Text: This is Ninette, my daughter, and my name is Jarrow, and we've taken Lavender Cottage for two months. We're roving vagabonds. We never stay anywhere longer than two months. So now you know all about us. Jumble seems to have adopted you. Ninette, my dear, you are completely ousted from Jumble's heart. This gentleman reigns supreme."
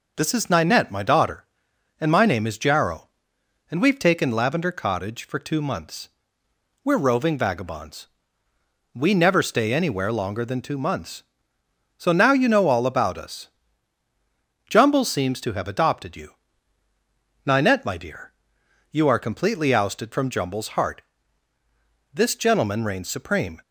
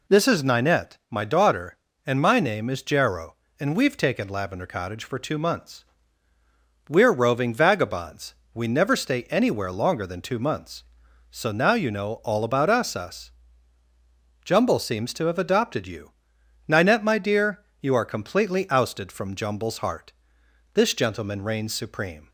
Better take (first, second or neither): first